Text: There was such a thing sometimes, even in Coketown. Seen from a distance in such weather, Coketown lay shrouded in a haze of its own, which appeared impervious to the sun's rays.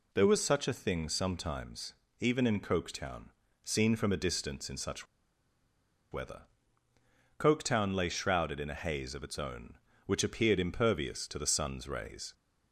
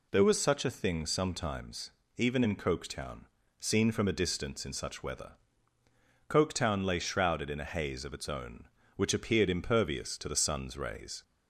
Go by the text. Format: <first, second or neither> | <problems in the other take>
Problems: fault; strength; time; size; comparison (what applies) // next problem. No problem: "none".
second | pauses between "such" and "weather"; at 5.0 s; 1.0 s long